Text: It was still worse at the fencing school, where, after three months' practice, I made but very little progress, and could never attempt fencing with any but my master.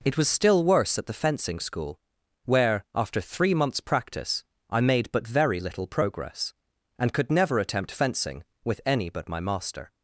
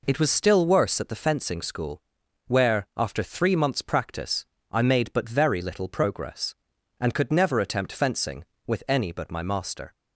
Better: neither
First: none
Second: none

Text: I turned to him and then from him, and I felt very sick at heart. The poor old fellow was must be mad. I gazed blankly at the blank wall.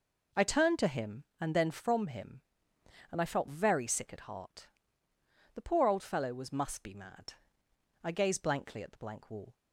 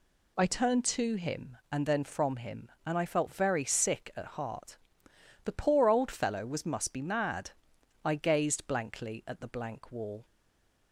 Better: first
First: none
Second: stays silent after the last word; slight; from 10.2 s on; 0.7 s long

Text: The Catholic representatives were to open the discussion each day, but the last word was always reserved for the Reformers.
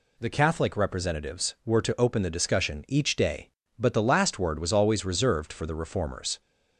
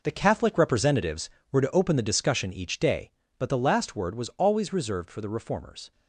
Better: first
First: none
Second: gets quieter; strong; throughout; 11 dB

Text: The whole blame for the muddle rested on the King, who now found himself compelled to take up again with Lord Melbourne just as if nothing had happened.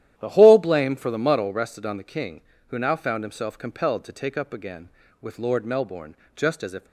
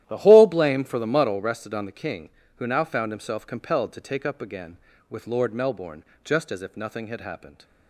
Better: second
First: starts louder than the rest; strong; until 1.1 s; 11.5 dB // pauses between "Melbourne" and "just"; slight; at 6.1 s; 0.20 s long // stops before "nothing had happened"; at 6.8 s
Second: starts louder than the rest; strong; until 1.0 s; 12.5 dB // pauses between "Melbourne" and "just"; slight; at 6.0 s; 0.20 s long

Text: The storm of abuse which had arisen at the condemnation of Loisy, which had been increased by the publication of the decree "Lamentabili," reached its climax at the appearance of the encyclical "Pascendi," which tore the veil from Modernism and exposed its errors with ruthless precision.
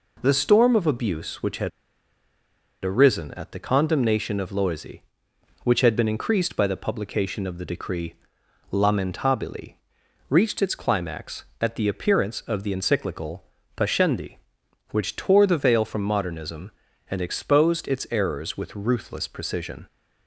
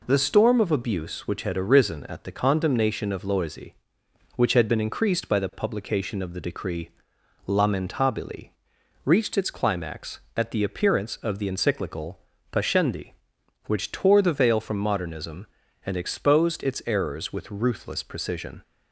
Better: second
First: pauses between "had" and "arisen"; at 1.6 s; 1.1 s long // pauses between "decree" and "Lamentabili"; noticeable; at 8.1 s; 0.58 s long // pauses between "encyclical" and "Pascendi"; slight; at 13.4 s; 0.32 s long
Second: pauses between "decree" and "Lamentabili"; noticeable; at 6.8 s; 0.58 s long // pauses between "encyclical" and "Pascendi"; slight; at 12.1 s; 0.32 s long

